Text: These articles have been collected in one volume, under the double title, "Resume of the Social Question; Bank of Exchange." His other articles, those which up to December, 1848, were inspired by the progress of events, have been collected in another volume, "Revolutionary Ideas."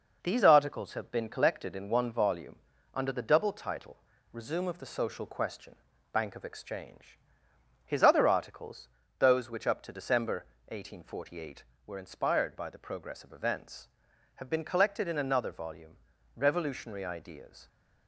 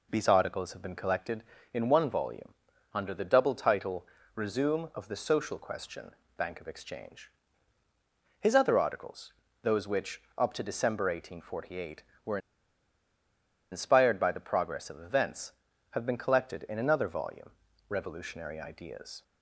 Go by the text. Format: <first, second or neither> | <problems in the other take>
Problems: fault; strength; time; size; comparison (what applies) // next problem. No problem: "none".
first | pauses between "which" and "up"; slight; at 10.1 s; 0.18 s long // pauses between "were" and "inspired"; strong; at 12.3 s; 1.3 s long